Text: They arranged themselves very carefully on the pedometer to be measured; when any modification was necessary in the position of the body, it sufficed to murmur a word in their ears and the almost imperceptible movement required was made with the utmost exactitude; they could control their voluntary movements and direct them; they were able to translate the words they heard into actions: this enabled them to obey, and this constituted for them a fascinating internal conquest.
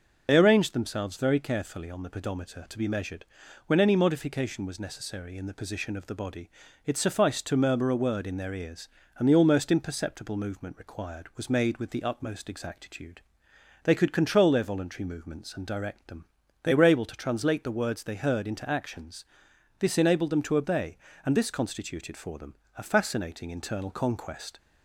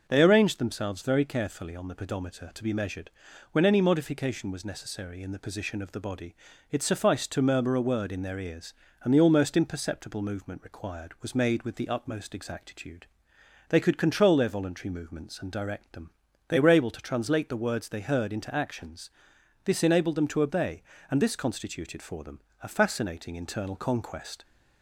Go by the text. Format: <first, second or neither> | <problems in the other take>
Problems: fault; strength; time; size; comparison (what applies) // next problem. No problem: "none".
second | loses the start of "They"; at 0.2 s; 50 ms // pauses between "them" and "a"; slight; at 22.5 s; 0.20 s long; slight in the second